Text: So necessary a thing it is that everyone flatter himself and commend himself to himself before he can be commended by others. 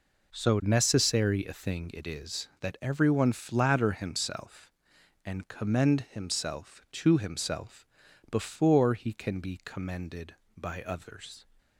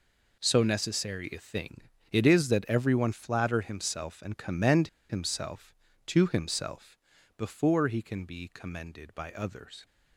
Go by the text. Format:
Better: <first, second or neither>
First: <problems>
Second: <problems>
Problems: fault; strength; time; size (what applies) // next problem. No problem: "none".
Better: first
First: pauses between "himself" and "before"; at 7.8 s; 0.44 s long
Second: pauses between "thing" and "it"; slight; at 1.8 s; 0.30 s long // pauses between "commend" and "himself"; slight; at 4.8 s; 0.22 s long // pauses between "himself" and "before"; at 6.9 s; 0.40 s long